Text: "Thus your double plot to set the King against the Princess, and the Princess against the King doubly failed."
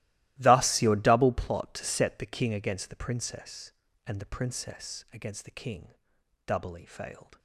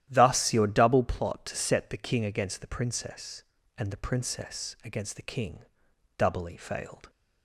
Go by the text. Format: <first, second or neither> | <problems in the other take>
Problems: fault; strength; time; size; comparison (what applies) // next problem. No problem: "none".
second | gets quieter; strong; throughout; 18 dB // starts louder than the rest; strong; until 1.3 s; 16.5 dB; strong in the second // pauses between "King" and "doubly"; noticeable; at 5.9 s; 0.52 s long; noticeable in the second